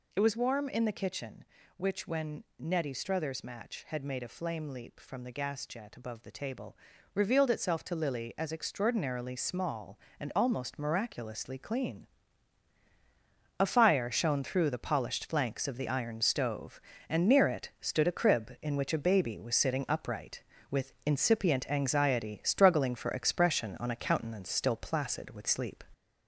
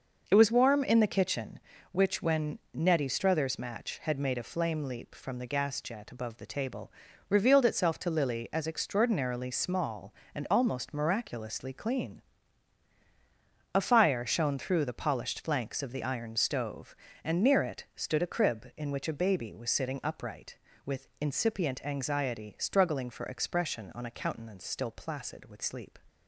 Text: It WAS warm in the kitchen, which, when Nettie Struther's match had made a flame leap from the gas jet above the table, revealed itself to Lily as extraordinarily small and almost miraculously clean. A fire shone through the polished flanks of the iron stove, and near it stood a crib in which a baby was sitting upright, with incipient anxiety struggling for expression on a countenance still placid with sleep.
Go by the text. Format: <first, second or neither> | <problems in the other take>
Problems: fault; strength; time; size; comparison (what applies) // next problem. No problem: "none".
second | gets louder; throughout; 3.5 dB // pauses between "when" and "Nettie"; slight; at 2.4 s; 0.16 s long; slight in the second